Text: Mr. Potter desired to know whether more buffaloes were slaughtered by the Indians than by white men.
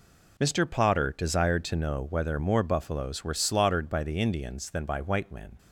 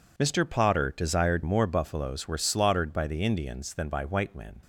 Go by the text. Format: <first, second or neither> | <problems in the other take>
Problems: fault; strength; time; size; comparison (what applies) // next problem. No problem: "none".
first | skips "to know whether"; at 1.4 s